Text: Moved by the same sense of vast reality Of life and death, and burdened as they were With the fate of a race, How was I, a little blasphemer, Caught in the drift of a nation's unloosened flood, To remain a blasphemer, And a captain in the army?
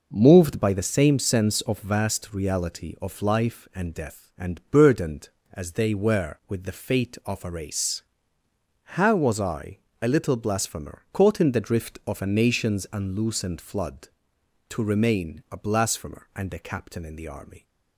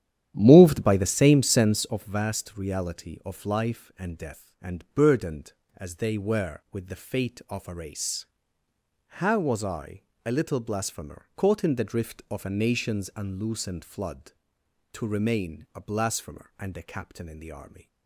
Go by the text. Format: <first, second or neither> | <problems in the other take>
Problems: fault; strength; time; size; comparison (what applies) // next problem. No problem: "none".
first | starts louder than the rest; strong; until 1.9 s; 10.5 dB